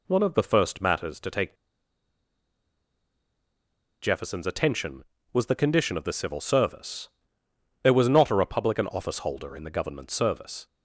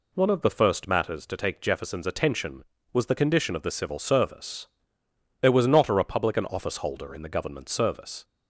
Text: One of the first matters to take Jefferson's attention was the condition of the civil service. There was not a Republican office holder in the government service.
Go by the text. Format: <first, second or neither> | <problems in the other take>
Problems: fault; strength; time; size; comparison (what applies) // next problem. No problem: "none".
second | pauses between "take" and "Jefferson's"; strong; at 1.5 s; 2.4 s long